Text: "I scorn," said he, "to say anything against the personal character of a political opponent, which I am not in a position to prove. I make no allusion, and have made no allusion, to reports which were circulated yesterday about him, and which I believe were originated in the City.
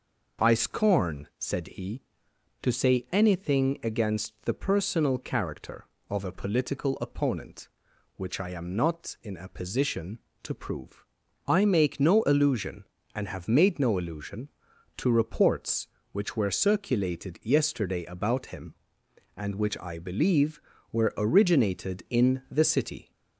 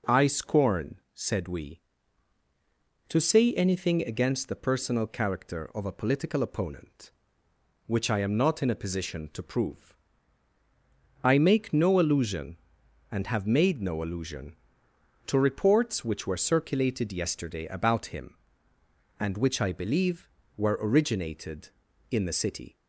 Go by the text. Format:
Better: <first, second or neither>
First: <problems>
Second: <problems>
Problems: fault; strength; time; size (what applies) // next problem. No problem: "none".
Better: first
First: none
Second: says "we" for "he"; at 1.4 s